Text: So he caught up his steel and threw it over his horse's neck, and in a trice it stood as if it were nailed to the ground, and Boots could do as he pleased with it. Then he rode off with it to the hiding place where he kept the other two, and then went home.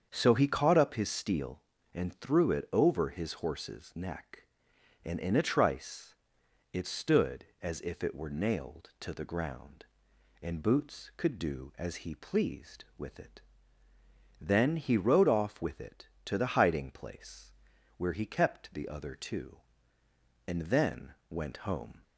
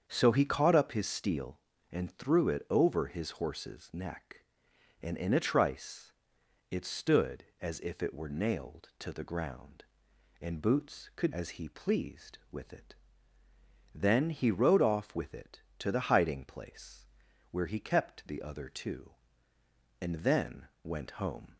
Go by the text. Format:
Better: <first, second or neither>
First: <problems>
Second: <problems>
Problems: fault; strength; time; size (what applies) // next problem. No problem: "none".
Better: first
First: starts louder than the rest; strong; until 1.1 s; 7.5 dB // pauses between "trice" and "it"; noticeable; at 6.1 s; 0.58 s long // pauses between "place" and "where"; at 17.5 s; 0.44 s long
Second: starts louder than the rest; strong; until 1.0 s; 7.5 dB // pauses between "trice" and "it"; noticeable; at 6.1 s; 0.58 s long // skips "do"; at 11.3 s // pauses between "place" and "where"; at 17.0 s; 0.44 s long